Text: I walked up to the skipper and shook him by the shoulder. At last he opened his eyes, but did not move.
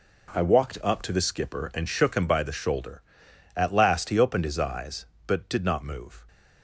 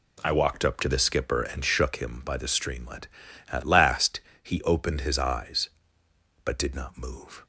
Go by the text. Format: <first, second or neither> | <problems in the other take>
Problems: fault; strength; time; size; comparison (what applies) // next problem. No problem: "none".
first | says "streamlet" for "shoulder"; at 2.4 s // pauses between "last" and "he"; slight; at 4.1 s; 0.24 s long